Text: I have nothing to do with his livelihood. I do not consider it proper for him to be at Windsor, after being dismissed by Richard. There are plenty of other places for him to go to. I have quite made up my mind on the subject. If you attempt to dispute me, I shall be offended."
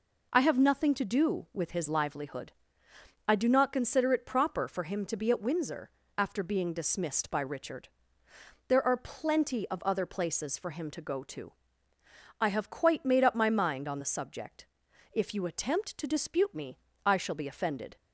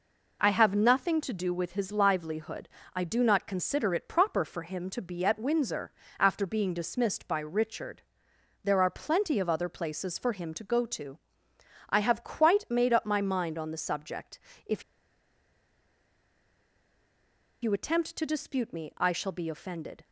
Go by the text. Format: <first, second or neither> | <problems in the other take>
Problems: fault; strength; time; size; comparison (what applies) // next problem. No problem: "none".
first | pauses between "If" and "you"; strong; at 14.8 s; 2.7 s long